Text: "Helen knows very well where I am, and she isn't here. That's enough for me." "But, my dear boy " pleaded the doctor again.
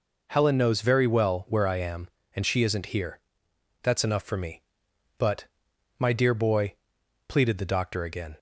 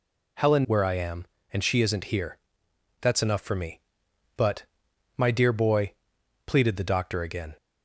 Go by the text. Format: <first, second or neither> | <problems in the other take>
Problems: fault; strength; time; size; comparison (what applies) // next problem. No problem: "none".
first | skips "knows very well"; at 0.6 s